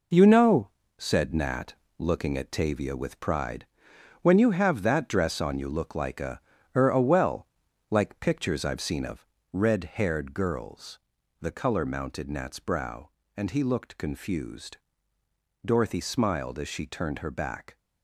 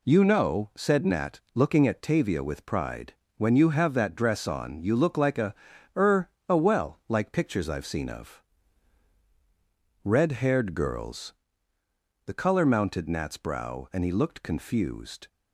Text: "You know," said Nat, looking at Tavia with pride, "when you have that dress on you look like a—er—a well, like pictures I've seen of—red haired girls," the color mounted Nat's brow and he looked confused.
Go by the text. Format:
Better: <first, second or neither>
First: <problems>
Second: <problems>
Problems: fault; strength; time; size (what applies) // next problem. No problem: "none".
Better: second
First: goes on to say "Dorothy smiled as she turned her back"; strong; from 15.6 s on; 2.1 s long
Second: none